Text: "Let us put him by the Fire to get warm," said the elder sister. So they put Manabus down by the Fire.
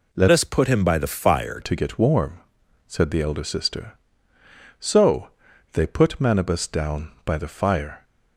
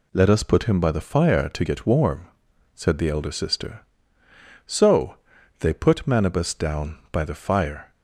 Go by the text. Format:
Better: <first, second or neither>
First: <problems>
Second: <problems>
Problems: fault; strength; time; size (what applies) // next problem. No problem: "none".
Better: second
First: changes voice from "us" to "Fire"; from 0.3 to 1.5 s; 1.2 s long // pauses between "So" and "they"; at 5.2 s; 0.42 s long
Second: pauses between "So" and "they"; at 5.1 s; 0.42 s long